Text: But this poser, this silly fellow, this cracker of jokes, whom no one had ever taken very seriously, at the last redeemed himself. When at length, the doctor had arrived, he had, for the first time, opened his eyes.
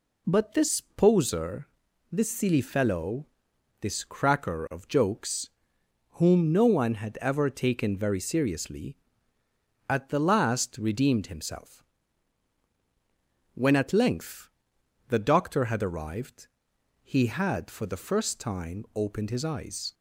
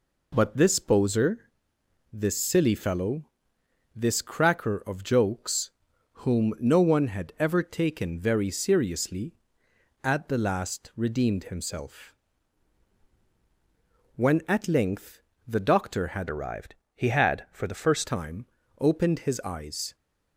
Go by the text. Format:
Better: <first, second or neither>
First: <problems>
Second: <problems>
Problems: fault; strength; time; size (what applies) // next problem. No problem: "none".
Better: first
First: none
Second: changes voice from "arrived" to "first"; from 16.2 to 18.0 s; 1.8 s long